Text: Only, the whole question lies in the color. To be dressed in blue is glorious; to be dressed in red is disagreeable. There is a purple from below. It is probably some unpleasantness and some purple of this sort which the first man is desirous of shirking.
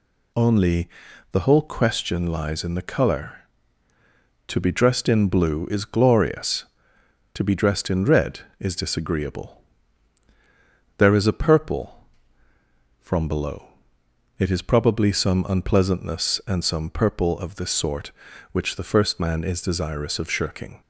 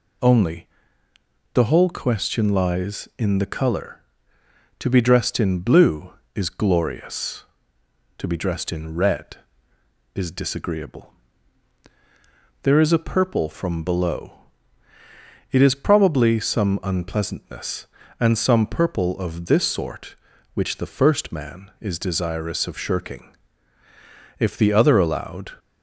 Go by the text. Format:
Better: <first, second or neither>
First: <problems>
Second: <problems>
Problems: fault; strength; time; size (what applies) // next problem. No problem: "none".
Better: first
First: none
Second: goes on to say "If the other allowed"; noticeable; from 24.3 s on; 1.1 s long